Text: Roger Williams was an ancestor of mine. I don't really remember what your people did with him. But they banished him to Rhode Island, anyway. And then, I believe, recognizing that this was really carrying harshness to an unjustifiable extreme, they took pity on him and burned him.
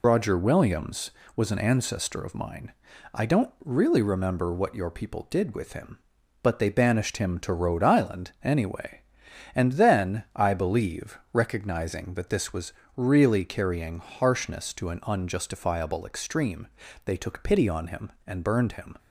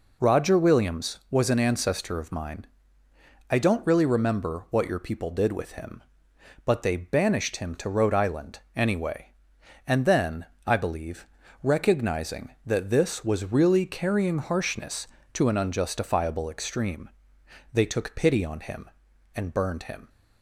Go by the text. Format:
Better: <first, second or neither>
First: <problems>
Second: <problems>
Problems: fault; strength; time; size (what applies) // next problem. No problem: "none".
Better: second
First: loses the start of "Roger"; at 0.0 s; 45 ms // pauses between "was" and "really"; slight; at 12.7 s; 0.24 s long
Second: none